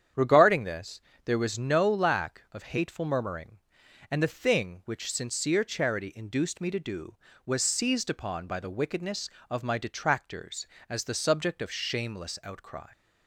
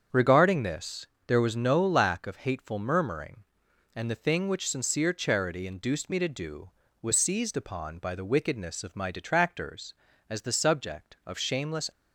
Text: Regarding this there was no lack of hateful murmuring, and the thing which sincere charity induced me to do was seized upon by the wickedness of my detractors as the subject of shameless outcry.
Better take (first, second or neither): first